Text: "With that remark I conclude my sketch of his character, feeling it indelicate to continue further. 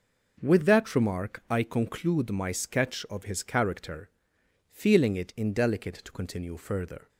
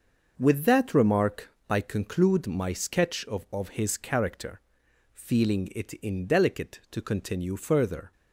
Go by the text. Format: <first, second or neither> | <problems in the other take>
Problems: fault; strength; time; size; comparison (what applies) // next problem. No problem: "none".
first | starts louder than the rest; noticeable; until 1.3 s; 6 dB // pauses between "remark" and "I"; slight; at 1.4 s; 0.20 s long // says "of" twice; at 3.5 s